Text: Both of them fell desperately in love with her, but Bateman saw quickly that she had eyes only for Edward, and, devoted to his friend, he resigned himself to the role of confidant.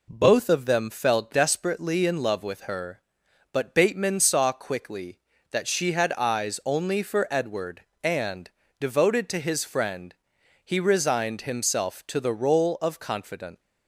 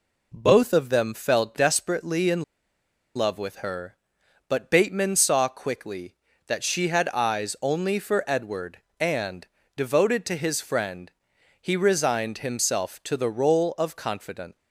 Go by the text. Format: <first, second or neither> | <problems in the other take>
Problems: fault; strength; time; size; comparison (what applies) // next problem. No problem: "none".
first | pauses between "in" and "love"; noticeable; at 2.4 s; 0.73 s long